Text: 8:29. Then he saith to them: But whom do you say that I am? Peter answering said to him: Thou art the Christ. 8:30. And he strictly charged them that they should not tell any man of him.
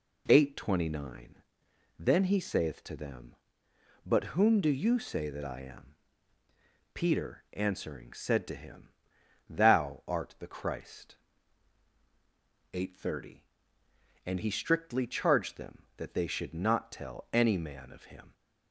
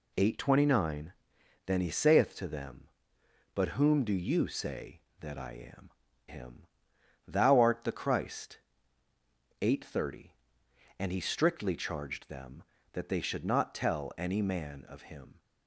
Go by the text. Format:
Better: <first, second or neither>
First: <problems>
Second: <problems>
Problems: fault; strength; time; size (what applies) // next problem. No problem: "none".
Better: first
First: none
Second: skips "Peter answering said to"; at 6.0 s